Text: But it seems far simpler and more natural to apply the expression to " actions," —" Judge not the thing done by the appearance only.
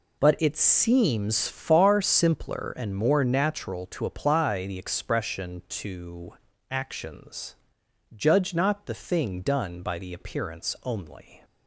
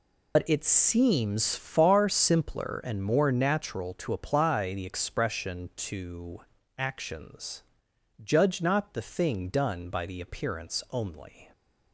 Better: first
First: none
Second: loses the start of "But"; at 0.3 s; 75 ms

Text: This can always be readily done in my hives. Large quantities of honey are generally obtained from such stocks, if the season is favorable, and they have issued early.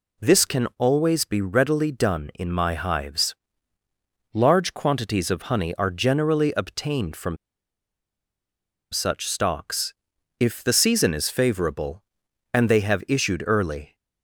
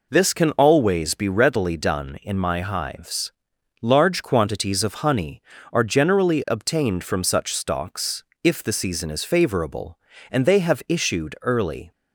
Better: second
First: pauses between "from" and "such"; strong; at 7.3 s; 1.5 s long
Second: none

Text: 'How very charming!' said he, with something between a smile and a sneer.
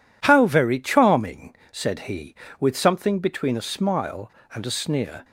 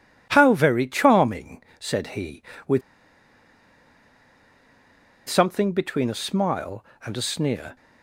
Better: first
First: none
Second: pauses between "with" and "something"; strong; at 2.8 s; 2.4 s long

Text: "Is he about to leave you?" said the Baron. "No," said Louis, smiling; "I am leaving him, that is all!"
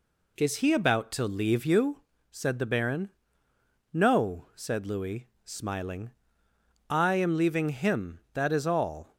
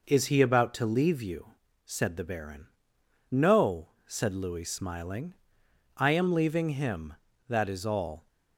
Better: neither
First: none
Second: none

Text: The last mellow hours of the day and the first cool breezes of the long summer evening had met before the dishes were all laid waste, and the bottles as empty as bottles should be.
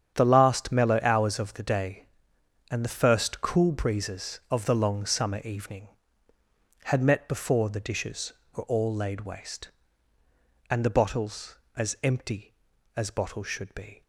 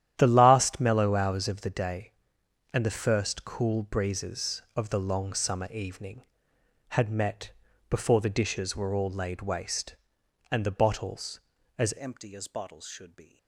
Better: first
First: starts louder than the rest; strong; until 1.1 s; 8.5 dB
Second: starts louder than the rest; strong; until 1.1 s; 11 dB // pauses between "met" and "before"; at 7.5 s; 0.40 s long // changes voice at "empty"; from 11.9 s on; 1.4 s long

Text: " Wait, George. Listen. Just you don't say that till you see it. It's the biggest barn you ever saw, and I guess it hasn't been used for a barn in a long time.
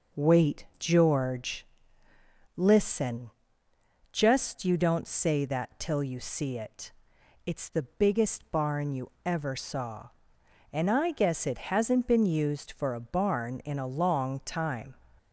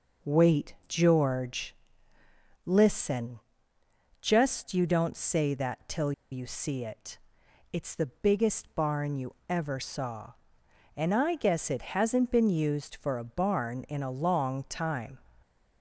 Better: first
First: none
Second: pauses between "till" and "you"; slight; at 6.1 s; 0.19 s long

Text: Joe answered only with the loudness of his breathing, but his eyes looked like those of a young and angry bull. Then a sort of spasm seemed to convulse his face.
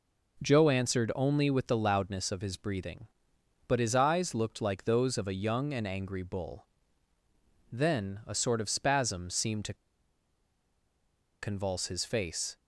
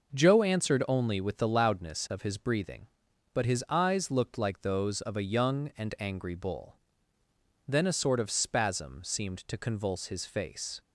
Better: second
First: pauses between "to" and "convulse"; strong; at 9.7 s; 1.6 s long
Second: none

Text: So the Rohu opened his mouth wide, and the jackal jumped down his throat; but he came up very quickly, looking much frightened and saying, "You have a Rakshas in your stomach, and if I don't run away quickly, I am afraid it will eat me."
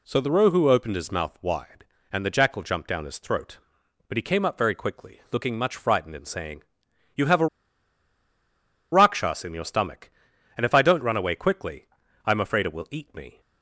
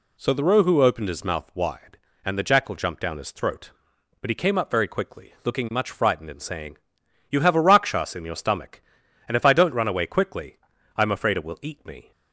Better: second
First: pauses between "a" and "Rakshas"; strong; at 7.4 s; 1.4 s long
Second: none

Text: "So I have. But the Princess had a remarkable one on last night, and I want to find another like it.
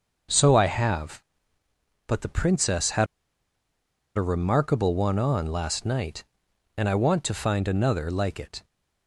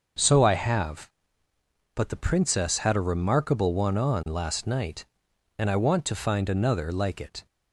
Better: second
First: starts louder than the rest; noticeable; until 2.1 s; 6 dB // pauses between "had" and "a"; at 3.0 s; 1.1 s long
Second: starts louder than the rest; noticeable; until 2.0 s; 6 dB

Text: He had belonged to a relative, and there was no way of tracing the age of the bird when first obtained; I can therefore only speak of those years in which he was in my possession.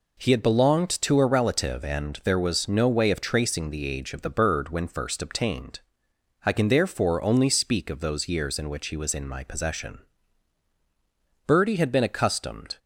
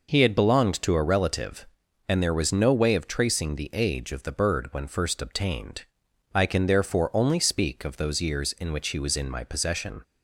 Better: second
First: goes on to say "Birdie had been accustomed"; from 11.4 s on; 1.3 s long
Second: none

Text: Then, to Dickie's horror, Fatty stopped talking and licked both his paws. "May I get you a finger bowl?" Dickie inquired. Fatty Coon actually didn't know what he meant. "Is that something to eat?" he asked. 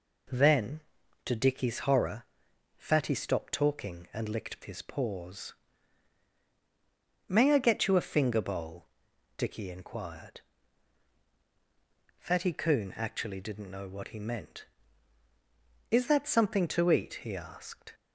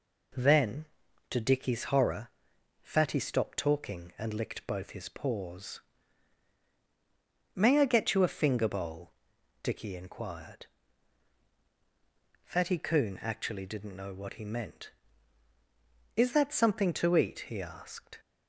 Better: second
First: skips "both"; at 4.6 s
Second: none

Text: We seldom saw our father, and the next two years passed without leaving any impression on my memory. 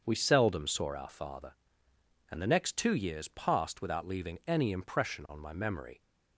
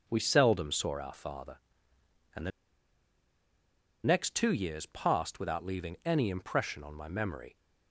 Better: first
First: starts louder than the rest; until 1.0 s; 6.5 dB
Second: starts louder than the rest; until 1.0 s; 7 dB // pauses between "the" and "next"; strong; at 2.5 s; 1.5 s long

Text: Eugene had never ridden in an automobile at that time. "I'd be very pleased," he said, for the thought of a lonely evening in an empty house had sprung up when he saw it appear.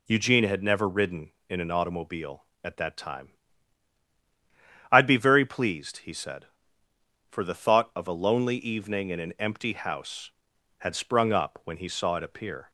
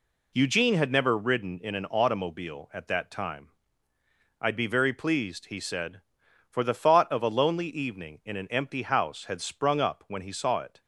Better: first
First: none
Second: stops before "appear"; at 10.8 s

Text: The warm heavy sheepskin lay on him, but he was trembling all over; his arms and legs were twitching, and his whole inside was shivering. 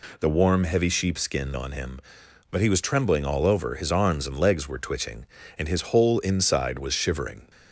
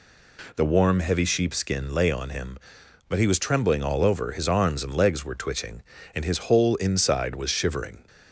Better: second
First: skips "lay"; at 1.5 s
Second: none

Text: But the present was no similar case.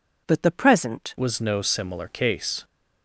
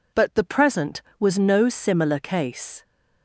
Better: second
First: changes voice at "was"; from 1.1 s on; 1.5 s long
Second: none

